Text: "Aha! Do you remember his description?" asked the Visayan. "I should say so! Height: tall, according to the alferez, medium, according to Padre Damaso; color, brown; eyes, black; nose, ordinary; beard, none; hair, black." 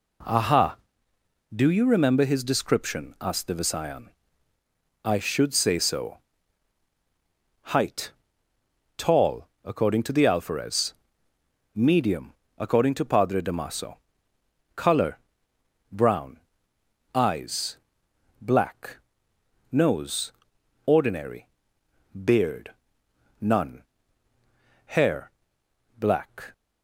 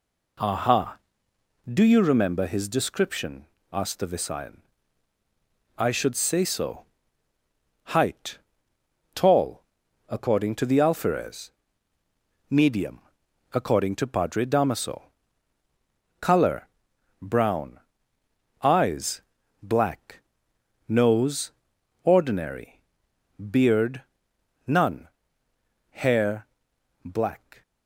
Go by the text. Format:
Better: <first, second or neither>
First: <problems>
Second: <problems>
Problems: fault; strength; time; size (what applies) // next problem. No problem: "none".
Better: neither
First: none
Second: none